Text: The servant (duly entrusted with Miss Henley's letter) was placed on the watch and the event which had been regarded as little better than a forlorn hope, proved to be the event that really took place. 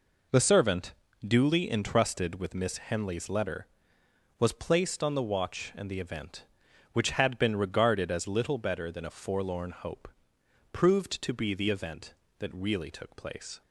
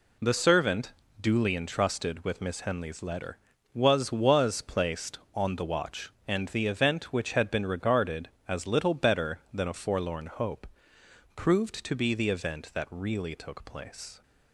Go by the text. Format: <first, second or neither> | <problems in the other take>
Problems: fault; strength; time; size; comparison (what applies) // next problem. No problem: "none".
first | says "was" twice; at 4.1 s